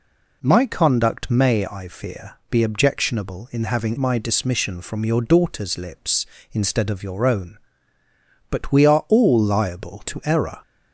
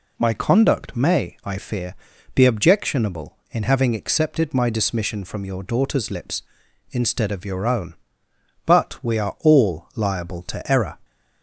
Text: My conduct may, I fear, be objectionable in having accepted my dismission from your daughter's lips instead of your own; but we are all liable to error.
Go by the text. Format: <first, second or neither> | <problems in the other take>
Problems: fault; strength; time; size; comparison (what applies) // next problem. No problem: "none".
second | skips "accepted"; at 3.9 s